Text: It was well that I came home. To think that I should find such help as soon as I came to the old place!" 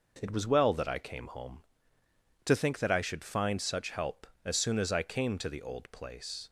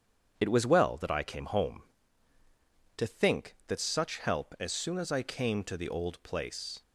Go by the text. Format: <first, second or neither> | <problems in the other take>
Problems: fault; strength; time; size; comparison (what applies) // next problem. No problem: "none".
first | starts louder than the rest; strong; until 1.3 s; 7.5 dB // skips "I should find"; at 3.7 s